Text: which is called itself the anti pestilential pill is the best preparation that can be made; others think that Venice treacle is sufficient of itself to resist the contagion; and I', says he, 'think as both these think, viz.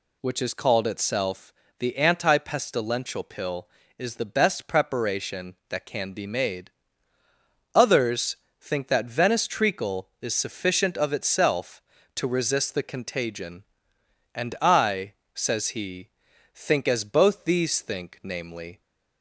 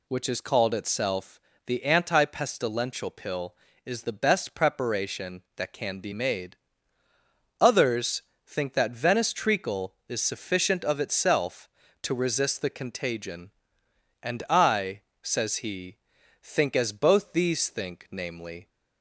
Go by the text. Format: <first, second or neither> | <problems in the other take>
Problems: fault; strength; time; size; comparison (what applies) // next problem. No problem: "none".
neither | pauses between "itself" and "the"; slight; the same in both // pauses between "others" and "think"; slight; the same in both